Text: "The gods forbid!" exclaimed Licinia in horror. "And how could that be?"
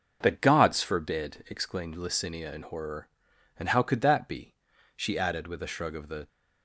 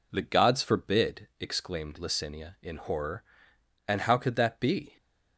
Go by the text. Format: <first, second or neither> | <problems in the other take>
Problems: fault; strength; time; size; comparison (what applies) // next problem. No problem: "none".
second | starts louder than the rest; noticeable; until 1.2 s; 6 dB // goes on to say "she added with a shrug of the"; from 4.9 s on; 1.3 s long